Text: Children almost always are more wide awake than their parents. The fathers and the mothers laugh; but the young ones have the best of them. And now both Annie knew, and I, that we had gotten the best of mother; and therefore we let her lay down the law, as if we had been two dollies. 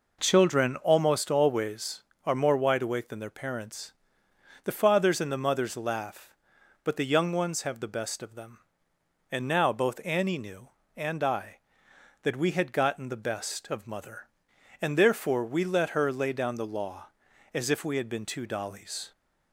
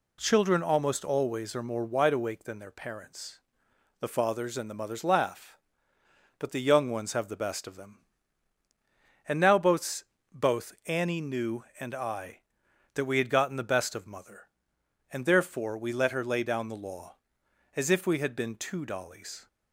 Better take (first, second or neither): first